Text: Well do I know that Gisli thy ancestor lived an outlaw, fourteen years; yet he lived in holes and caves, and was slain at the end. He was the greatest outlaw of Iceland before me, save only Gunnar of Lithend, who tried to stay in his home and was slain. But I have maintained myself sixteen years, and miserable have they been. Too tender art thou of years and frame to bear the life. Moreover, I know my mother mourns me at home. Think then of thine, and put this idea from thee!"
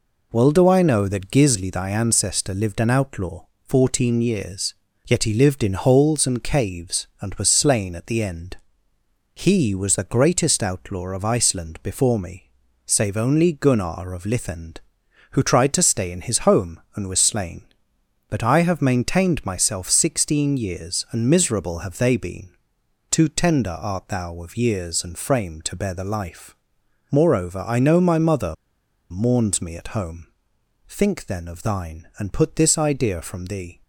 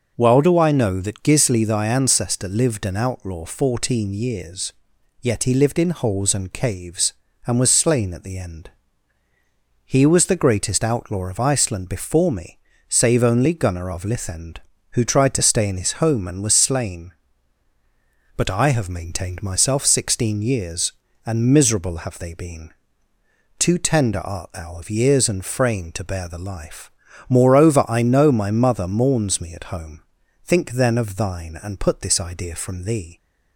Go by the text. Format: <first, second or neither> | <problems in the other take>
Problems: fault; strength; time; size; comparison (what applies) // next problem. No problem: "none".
second | pauses between "mother" and "mourns"; noticeable; at 28.5 s; 0.57 s long